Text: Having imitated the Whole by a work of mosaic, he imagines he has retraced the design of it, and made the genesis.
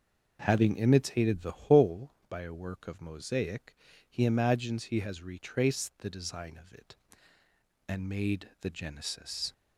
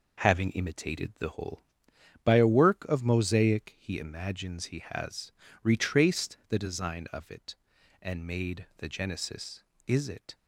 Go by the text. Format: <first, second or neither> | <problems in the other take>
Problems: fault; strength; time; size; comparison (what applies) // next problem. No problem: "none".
first | pauses between "has" and "retraced"; slight; at 5.3 s; 0.32 s long // goes on to say "Is it"; slight; from 9.8 s on; 0.48 s long